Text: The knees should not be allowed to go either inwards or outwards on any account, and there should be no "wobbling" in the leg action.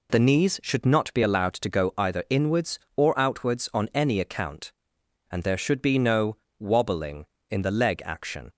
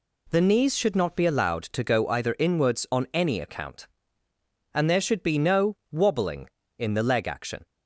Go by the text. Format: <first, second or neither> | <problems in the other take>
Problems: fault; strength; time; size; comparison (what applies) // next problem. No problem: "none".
first | skips "or outwards"; at 2.8 s // pauses between "no" and "wobbling"; slight; at 5.7 s; 0.16 s long; slight in the first